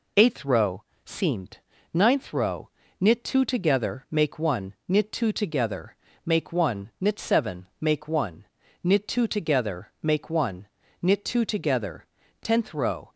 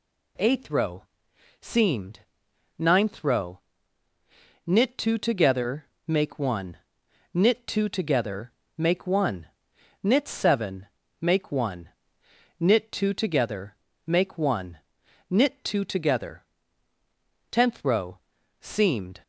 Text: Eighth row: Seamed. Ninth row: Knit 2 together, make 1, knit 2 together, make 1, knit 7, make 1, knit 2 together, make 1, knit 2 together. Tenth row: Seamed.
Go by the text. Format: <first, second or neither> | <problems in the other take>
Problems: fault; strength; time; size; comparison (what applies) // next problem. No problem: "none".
second | stops before "Seamed"; at 13.1 s